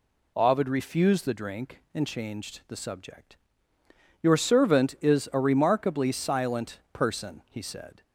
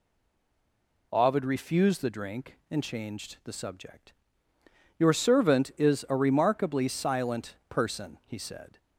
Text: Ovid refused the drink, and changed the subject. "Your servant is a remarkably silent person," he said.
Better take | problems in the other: first | stays silent before the first word; until 1.1 s; 1.1 s long

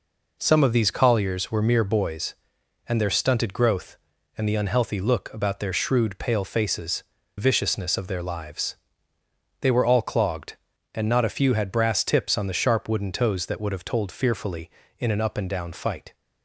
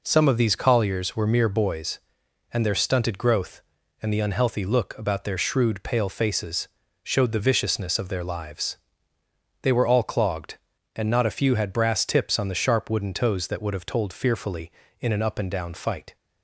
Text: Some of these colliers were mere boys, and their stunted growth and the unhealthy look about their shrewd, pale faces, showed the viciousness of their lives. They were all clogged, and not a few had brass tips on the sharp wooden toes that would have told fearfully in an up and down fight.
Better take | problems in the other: second | skips "showed the"; at 7.1 s

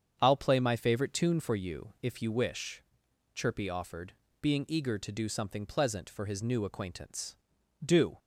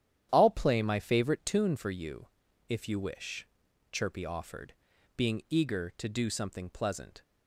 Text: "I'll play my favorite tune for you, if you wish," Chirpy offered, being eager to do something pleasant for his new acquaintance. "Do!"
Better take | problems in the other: first | starts louder than the rest; strong; until 1.3 s; 10 dB; strong in the first // stops before "for his new acquaintance Do"; at 7.2 s

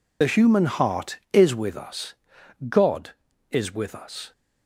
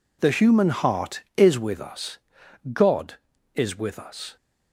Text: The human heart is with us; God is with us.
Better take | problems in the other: second | loses the start of "The"; at 0.2 s; 50 ms

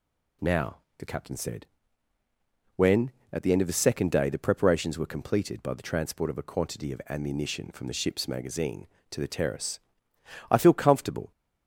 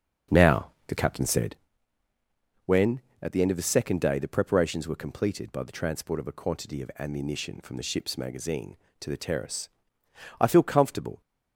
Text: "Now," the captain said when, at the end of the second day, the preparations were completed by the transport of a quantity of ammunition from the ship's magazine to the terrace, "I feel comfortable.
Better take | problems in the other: first | starts louder than the rest; until 1.8 s; 6.5 dB // pauses between "said" and "when"; at 1.5 s; 1.1 s long; also in the first

